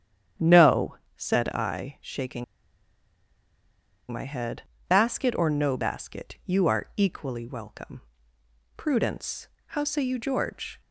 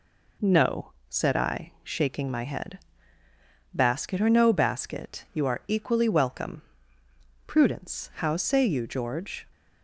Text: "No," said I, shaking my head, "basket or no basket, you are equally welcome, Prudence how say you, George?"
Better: second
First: starts louder than the rest; strong; until 1.5 s; 9 dB // pauses between "shaking" and "my"; strong; at 2.4 s; 1.6 s long // pauses between "Prudence" and "how"; slight; at 9.4 s; 0.18 s long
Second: none

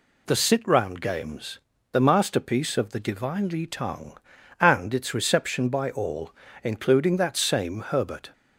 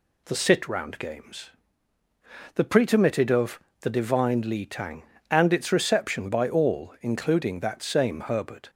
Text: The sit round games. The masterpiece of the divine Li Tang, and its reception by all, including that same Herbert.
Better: first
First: none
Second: says "pretermitted" for "masterpiece"; at 2.6 s // pauses between "of" and "the"; slight; at 3.5 s; 0.20 s long

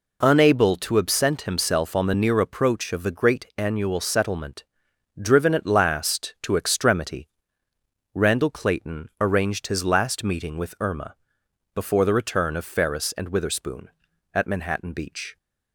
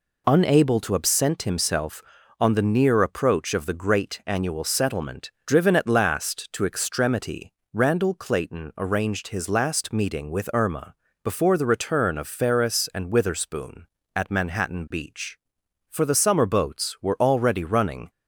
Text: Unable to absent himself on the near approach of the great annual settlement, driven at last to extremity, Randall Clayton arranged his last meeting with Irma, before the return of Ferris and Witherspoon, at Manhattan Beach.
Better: first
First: none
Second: goes on to say "For the summer boats were already running"; strong; from 15.8 s on; 2.2 s long

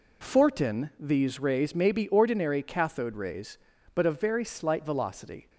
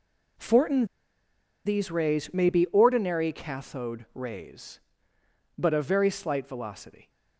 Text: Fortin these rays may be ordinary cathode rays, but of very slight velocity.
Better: first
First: none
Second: pauses between "Fortin" and "these"; noticeable; at 0.8 s; 0.80 s long

